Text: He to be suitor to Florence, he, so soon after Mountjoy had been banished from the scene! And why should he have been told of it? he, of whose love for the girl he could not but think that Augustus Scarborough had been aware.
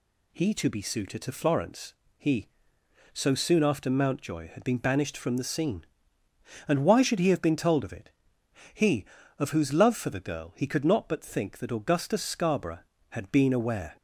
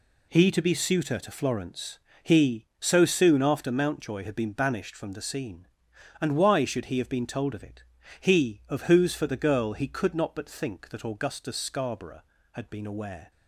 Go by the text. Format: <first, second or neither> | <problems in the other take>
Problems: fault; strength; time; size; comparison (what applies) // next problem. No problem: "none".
first | skips "love"; at 9.1 s